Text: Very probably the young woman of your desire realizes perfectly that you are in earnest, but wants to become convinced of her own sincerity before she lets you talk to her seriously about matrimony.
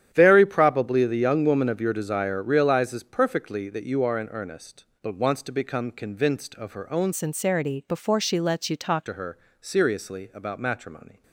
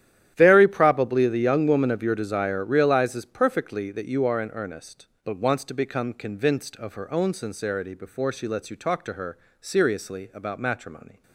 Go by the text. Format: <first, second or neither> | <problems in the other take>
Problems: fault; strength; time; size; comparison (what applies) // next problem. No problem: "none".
second | starts louder than the rest; strong; until 1.1 s; 10 dB; strong in the second // changes voice from "sincerity" to "talk"; from 7.1 to 9.0 s; 1.9 s long // pauses between "her" and "seriously"; slight; at 9.3 s; 0.24 s long; slight in the second